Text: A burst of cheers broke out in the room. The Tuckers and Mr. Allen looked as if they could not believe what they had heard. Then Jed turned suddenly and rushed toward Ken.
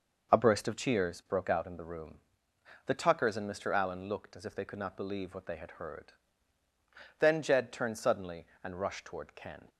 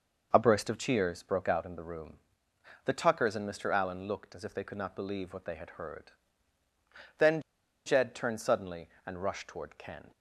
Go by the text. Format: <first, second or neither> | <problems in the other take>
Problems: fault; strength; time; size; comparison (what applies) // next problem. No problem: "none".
first | pauses between "Then" and "Jed"; at 7.4 s; 0.44 s long